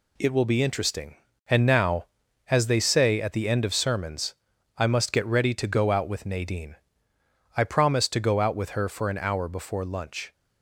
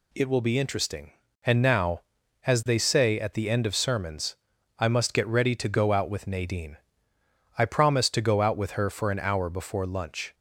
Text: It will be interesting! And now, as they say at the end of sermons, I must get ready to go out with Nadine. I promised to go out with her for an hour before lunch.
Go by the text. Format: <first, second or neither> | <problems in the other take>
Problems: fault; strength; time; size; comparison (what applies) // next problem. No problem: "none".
second | gets quieter; noticeable; throughout; 6 dB